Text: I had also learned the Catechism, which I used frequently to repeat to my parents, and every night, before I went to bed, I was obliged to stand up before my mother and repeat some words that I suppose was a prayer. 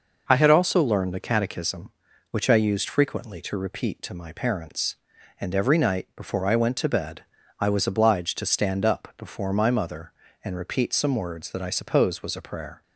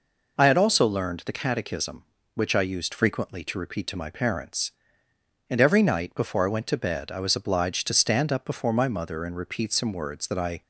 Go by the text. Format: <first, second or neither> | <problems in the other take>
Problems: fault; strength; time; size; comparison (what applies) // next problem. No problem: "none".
first | stops before "suppose was a prayer"; at 10.6 s